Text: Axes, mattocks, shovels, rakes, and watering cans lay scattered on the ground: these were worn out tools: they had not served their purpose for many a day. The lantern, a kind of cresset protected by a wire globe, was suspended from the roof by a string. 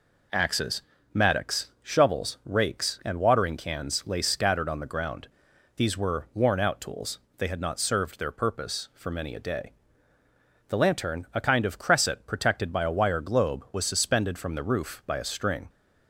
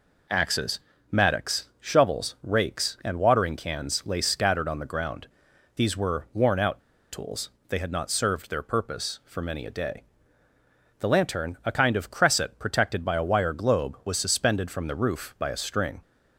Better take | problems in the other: first | pauses between "out" and "tools"; slight; at 6.8 s; 0.33 s long

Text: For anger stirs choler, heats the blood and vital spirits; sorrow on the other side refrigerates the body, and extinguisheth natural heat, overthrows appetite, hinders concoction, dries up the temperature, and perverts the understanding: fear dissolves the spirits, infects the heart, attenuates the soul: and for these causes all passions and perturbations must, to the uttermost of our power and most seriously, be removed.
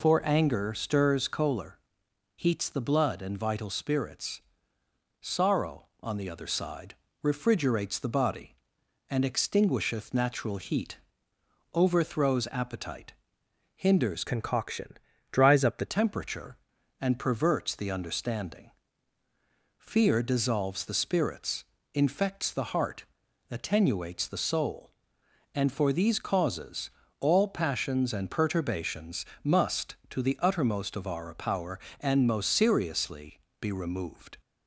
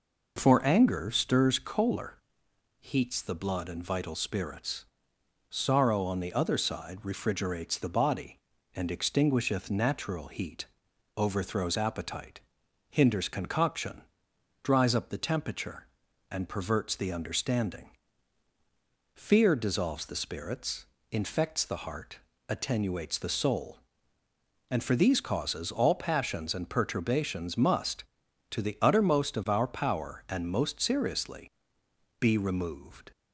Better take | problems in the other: second | pauses between "side" and "refrigerates"; slight; at 6.9 s; 0.26 s long // changes voice from "concoction" to "the"; from 14.2 to 15.8 s; 1.6 s long // pauses between "causes" and "all"; slight; at 26.8 s; 0.28 s long // pauses between "perturbations" and "must"; slight; at 29.2 s; 0.18 s long

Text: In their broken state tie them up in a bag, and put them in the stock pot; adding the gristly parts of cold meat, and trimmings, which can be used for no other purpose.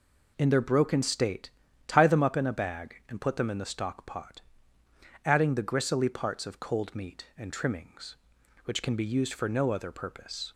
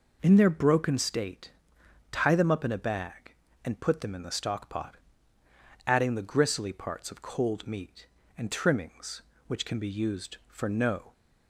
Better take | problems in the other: first | pauses between "state" and "tie"; noticeable; at 1.5 s; 0.60 s long; slight in the first // stops before "other purpose"; at 11.1 s

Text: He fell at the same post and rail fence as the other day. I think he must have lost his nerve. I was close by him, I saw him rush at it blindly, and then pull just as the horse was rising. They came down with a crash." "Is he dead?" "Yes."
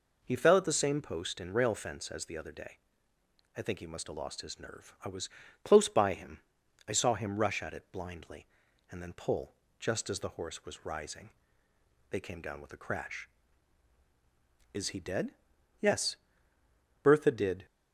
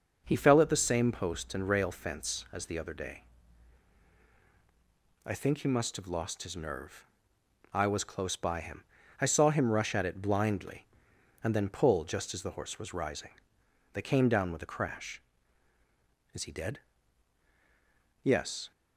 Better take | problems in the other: second | pauses between "was" and "close"; slight; at 5.2 s; 0.34 s long // pauses between "pull" and "just"; slight; at 9.5 s; 0.24 s long // goes on to say "Bertha did"; noticeable; from 17.0 s on; 0.64 s long

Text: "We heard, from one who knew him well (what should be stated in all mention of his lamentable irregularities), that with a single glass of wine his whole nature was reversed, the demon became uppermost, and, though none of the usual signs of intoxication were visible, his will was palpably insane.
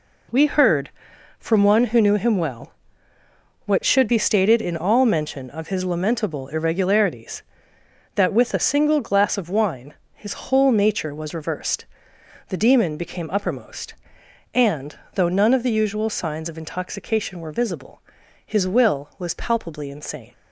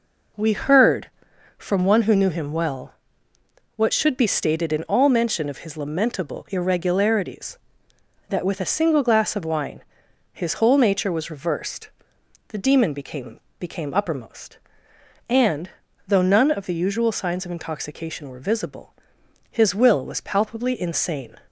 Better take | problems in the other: first | pauses between "wine" and "his"; noticeable; at 9.8 s; 0.48 s long; slight in the first // says "became" twice; at 13.5 s

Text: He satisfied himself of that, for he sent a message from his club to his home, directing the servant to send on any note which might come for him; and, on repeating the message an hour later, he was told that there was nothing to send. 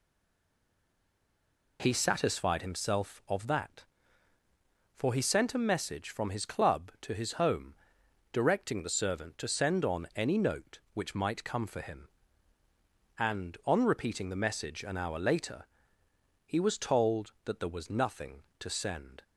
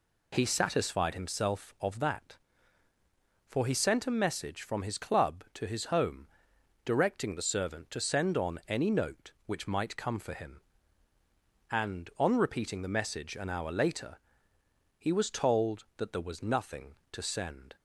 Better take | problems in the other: second | stays silent before the first word; noticeable; until 1.7 s; 1.7 s long

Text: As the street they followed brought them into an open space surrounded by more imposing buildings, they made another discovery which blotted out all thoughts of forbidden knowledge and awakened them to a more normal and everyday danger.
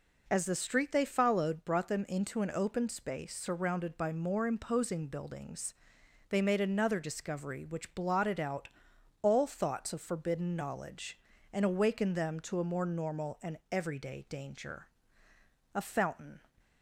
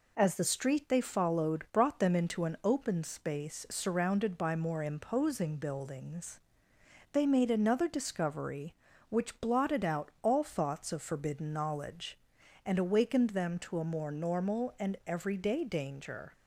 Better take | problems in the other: second | pauses between "out" and "all"; noticeable; at 8.6 s; 0.54 s long // goes on to say "A fountain"; noticeable; from 15.7 s on; 0.68 s long

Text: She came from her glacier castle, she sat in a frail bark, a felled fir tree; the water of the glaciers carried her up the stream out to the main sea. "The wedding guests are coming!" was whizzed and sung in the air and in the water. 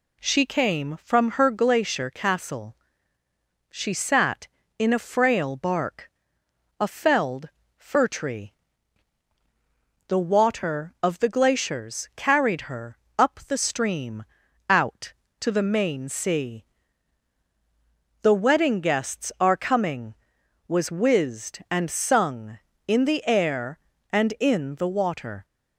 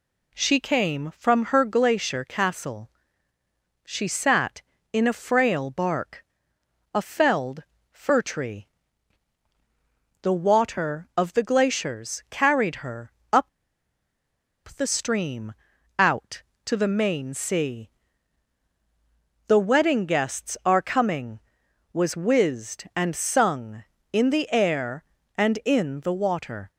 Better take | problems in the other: first | pauses between "felled" and "fir"; slight; at 7.6 s; 0.26 s long; slight in the first // pauses between "her" and "up"; slight; at 13.1 s; 0.20 s long; slight in the first // pauses between "up" and "the"; strong; at 13.4 s; 1.2 s long // pauses between "stream" and "out"; at 15.5 s; 0.44 s long; also in the first

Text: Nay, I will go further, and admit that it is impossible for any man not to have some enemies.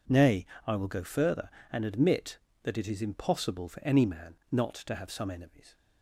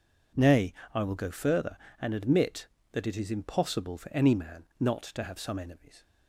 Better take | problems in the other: neither | pauses between "man" and "not"; slight; the same in both

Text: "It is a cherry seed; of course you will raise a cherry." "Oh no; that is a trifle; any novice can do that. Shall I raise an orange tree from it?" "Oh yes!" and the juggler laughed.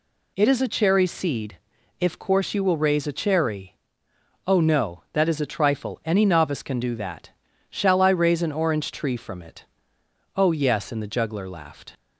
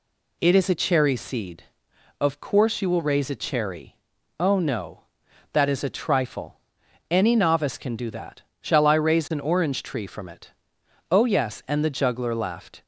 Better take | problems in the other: second | says "if" for "of"; at 1.9 s

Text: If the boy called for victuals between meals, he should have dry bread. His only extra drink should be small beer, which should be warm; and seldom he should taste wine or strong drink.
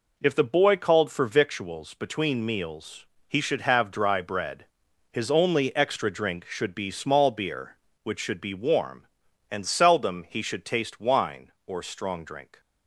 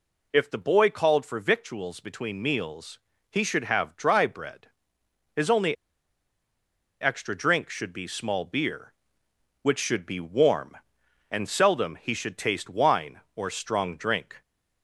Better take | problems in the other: first | pauses between "only" and "extra"; strong; at 5.7 s; 1.2 s long

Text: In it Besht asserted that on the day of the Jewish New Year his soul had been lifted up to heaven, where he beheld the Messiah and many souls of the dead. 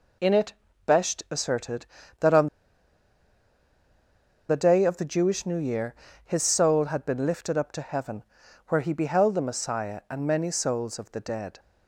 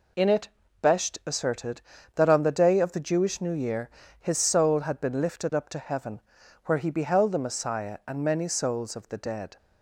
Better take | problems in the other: second | pauses between "it" and "Besht"; slight; at 0.5 s; 0.34 s long; slight in the second // pauses between "on" and "the"; strong; at 2.4 s; 2.0 s long // pauses between "Year" and "his"; slight; at 5.9 s; 0.30 s long; slight in the second

